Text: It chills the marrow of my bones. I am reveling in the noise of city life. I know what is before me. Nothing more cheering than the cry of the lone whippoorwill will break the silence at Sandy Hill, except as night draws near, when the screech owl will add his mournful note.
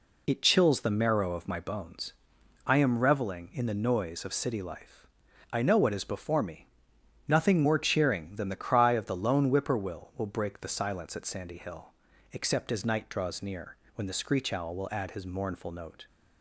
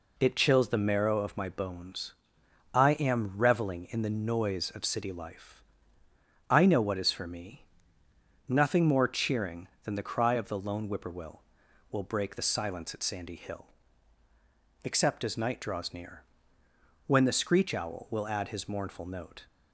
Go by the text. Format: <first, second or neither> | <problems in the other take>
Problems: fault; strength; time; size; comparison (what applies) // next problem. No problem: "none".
first | says "for" for "before"; at 7.1 s